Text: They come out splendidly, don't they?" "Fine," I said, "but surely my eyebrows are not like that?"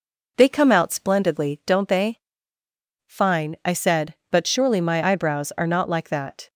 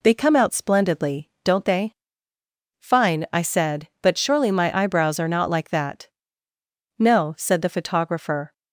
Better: first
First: none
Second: goes on to say "No said the photographer"; from 6.9 s on; 1.5 s long

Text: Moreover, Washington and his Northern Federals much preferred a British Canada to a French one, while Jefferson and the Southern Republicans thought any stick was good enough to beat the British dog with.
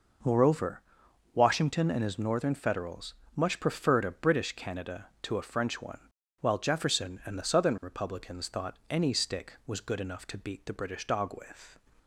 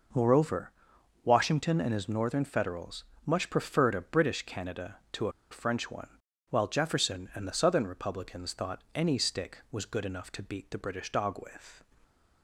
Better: first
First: pauses between "Federals" and "much"; slight; at 3.1 s; 0.20 s long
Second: pauses between "Federals" and "much"; slight; at 3.0 s; 0.20 s long // pauses between "a" and "French"; slight; at 5.3 s; 0.19 s long

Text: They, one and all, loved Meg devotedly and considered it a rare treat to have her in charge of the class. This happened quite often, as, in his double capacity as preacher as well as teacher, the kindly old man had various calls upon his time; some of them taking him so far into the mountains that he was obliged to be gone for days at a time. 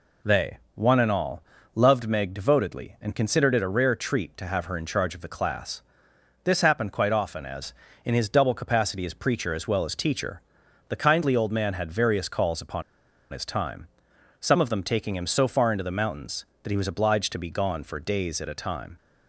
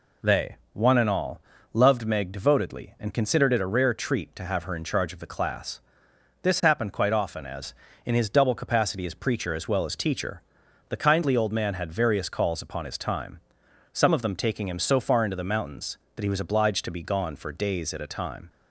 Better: second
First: pauses between "upon" and "his"; noticeable; at 12.8 s; 0.50 s long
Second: none

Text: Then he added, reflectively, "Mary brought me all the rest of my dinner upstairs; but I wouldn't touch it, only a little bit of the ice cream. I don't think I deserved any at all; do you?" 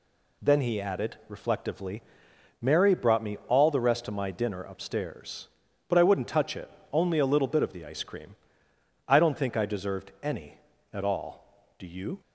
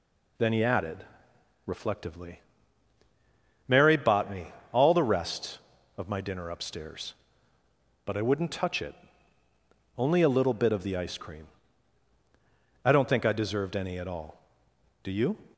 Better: first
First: none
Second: says "bought" for "brought"; at 3.9 s // pauses between "me" and "all"; slight; at 4.5 s; 0.22 s long

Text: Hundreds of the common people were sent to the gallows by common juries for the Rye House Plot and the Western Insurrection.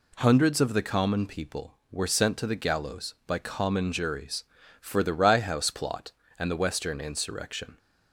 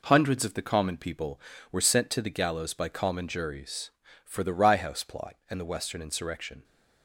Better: neither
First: none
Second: none

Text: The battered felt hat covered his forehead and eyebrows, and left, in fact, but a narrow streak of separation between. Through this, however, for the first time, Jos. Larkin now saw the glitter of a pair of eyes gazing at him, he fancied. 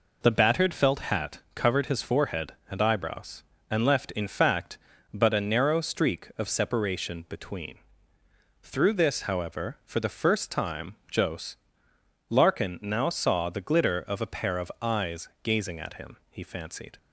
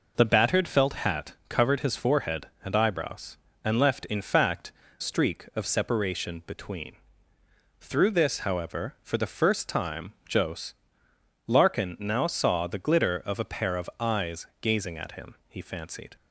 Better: first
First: pauses between "hat" and "covered"; slight; at 1.3 s; 0.16 s long // pauses between "eyes" and "gazing"; slight; at 15.2 s; 0.16 s long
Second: pauses between "hat" and "covered"; slight; at 1.3 s; 0.16 s long // skips "but a narrow"; at 4.8 s // pauses between "eyes" and "gazing"; slight; at 14.4 s; 0.16 s long

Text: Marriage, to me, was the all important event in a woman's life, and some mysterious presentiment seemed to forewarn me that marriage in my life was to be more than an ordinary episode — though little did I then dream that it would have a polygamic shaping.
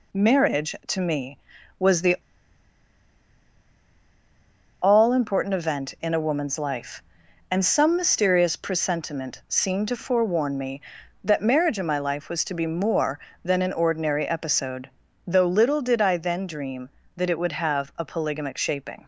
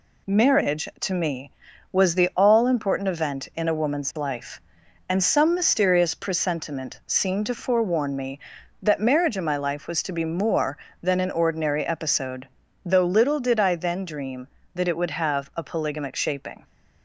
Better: second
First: pauses between "the" and "all"; strong; at 2.1 s; 2.6 s long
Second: none

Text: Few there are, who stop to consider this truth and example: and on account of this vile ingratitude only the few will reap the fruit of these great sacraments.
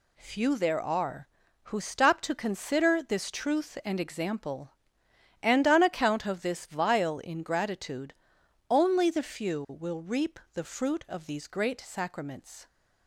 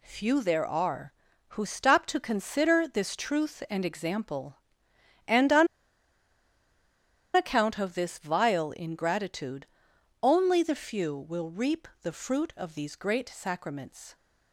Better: first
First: pauses between "ingratitude" and "only"; noticeable; at 8.1 s; 0.56 s long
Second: pauses between "on" and "account"; strong; at 5.6 s; 1.6 s long // pauses between "ingratitude" and "only"; noticeable; at 9.6 s; 0.56 s long

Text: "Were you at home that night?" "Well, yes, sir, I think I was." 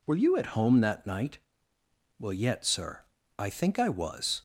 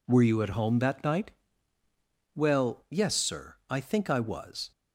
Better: second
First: says "yet" for "yes"; at 2.3 s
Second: none

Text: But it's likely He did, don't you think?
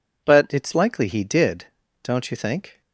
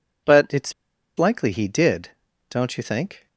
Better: first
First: none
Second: pauses between "it's" and "likely"; at 0.7 s; 0.44 s long

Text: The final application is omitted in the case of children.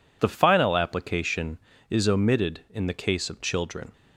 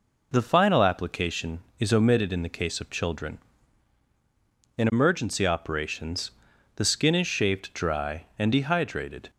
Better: first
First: none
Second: goes on to say "In emergency operations the skin is shaved dry and dehydrated"; strong; from 4.7 s on; 4.5 s long

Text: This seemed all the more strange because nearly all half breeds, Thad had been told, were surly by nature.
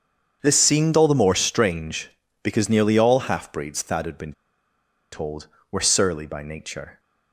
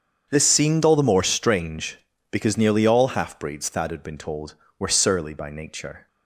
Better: second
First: starts louder than the rest; strong; until 1.4 s; 7 dB // pauses between "been" and "told"; noticeable; at 4.3 s; 0.80 s long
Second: starts louder than the rest; strong; until 1.3 s; 7 dB

